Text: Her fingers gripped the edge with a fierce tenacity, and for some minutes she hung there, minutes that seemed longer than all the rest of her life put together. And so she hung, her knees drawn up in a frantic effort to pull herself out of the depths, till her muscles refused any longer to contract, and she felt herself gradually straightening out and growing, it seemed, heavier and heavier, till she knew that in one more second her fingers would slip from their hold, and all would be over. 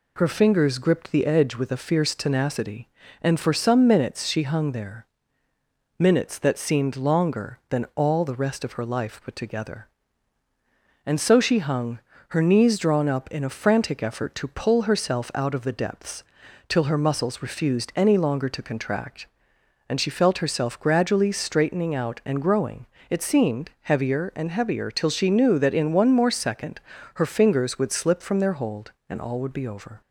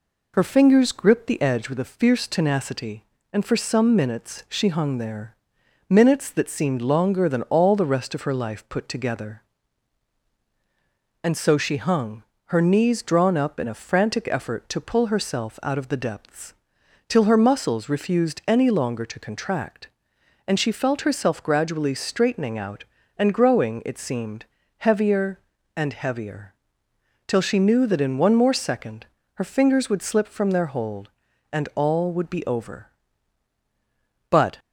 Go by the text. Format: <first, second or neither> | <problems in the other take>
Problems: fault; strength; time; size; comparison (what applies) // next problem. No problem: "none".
first | pauses between "second" and "her"; slight; at 29.0 s; 0.30 s long; slight in the first // goes on to say "But"; slight; from 34.3 s on; 0.28 s long